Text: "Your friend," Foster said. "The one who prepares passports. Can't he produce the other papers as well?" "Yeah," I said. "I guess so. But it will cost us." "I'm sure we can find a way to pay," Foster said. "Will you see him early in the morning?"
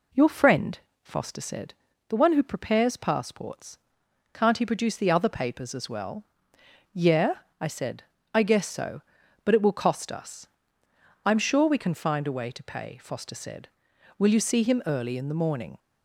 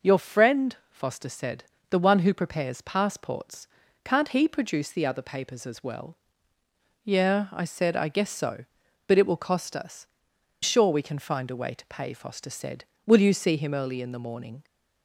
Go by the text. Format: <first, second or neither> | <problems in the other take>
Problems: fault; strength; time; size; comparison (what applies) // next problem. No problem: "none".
first | skips "I'm"; at 10.3 s